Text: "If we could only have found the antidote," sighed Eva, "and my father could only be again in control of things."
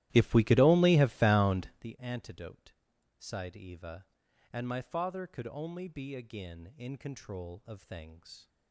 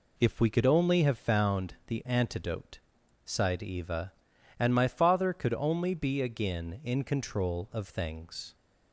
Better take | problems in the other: second | starts louder than the rest; strong; until 1.9 s; 15 dB

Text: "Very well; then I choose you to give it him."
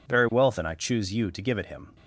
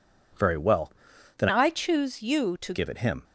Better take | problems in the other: first | changes voice from "I" to "to"; from 1.4 to 2.7 s; 1.3 s long

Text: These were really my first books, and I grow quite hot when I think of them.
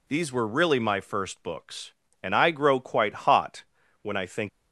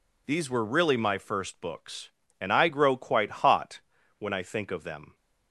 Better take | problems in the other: second | pauses between "hot" and "when"; at 3.6 s; 0.38 s long; also in the second // stops before "of them"; at 4.4 s

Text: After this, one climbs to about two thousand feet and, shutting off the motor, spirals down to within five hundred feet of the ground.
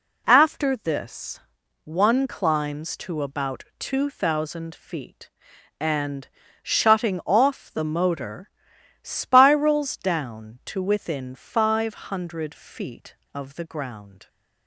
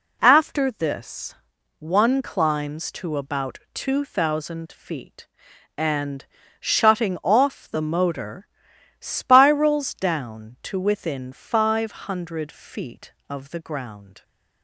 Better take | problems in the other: neither | pauses between "five" and "hundred"; slight; the same in both

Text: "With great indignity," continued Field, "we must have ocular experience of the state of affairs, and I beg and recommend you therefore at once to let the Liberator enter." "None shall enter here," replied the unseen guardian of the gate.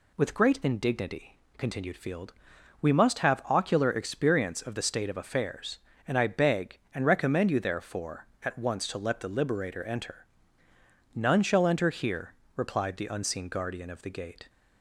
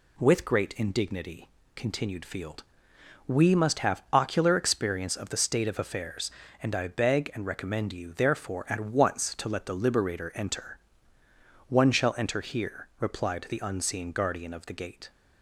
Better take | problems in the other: first | says "One" for "None"; at 11.6 s

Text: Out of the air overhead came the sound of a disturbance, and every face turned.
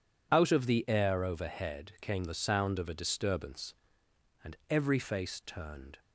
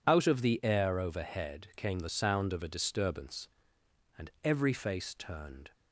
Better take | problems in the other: neither | none

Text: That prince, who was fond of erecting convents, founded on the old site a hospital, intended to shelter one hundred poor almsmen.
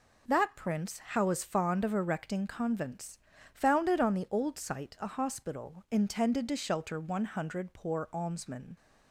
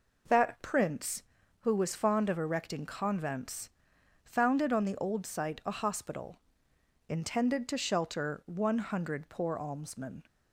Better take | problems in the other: second | says "how" for "who"; at 0.9 s

